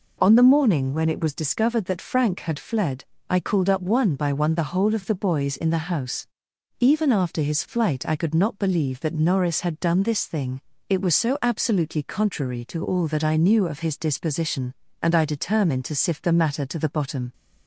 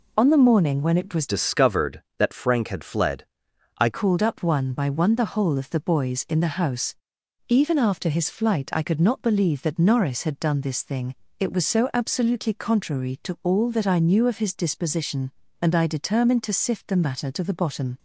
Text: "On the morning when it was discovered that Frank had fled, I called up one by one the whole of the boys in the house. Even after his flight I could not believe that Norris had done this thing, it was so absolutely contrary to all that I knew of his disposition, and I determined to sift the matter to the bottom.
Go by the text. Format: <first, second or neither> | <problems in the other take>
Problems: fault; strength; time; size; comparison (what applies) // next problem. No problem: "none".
first | changes voice from "discovered" to "I"; from 1.2 to 3.8 s; 2.6 s long